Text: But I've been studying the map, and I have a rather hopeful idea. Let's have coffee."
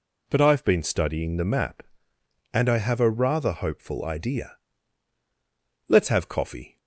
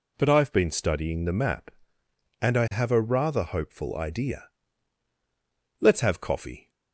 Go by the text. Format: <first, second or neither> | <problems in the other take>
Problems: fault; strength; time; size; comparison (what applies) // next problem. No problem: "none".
neither | none